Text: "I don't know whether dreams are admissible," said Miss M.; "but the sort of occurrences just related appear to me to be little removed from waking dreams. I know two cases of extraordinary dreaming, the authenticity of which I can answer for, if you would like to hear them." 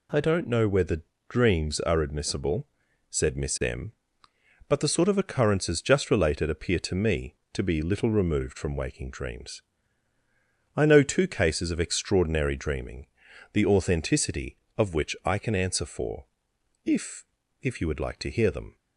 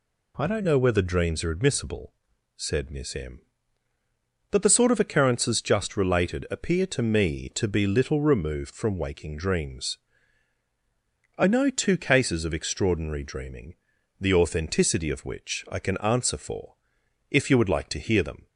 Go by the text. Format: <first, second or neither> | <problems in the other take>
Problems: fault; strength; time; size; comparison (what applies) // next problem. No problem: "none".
second | pauses between "whether" and "dreams"; slight; at 1.0 s; 0.26 s long // says "if" twice; at 17.6 s